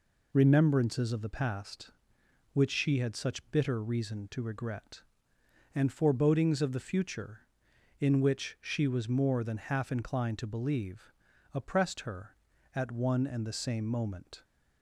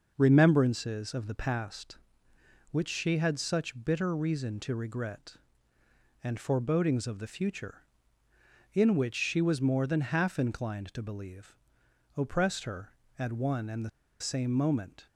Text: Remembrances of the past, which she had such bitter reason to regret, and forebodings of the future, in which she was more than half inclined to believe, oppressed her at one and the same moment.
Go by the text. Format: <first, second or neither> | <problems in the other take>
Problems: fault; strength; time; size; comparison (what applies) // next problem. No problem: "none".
first | pauses between "the" and "same"; slight; at 13.8 s; 0.30 s long